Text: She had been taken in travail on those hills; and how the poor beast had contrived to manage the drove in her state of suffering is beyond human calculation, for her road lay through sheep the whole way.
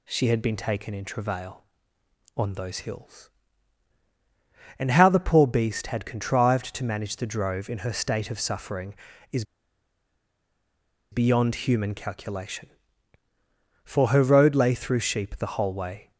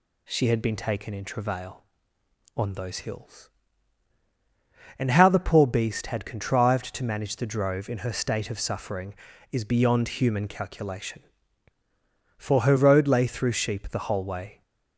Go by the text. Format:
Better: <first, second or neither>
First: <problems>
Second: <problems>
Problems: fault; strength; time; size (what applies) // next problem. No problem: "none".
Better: second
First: pauses between "is" and "beyond"; strong; at 9.4 s; 1.6 s long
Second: none